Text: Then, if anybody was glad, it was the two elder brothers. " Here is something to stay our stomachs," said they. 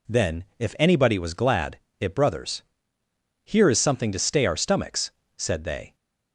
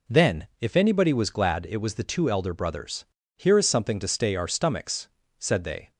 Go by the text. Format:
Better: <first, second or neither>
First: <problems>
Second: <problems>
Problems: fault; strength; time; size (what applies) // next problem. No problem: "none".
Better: second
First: skips "was the two elder"; at 2.1 s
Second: none